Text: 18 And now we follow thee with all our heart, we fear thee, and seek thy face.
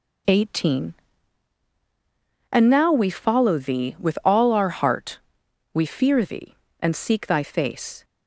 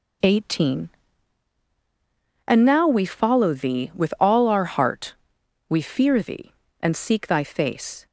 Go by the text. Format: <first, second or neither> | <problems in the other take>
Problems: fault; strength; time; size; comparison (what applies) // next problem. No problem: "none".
neither | none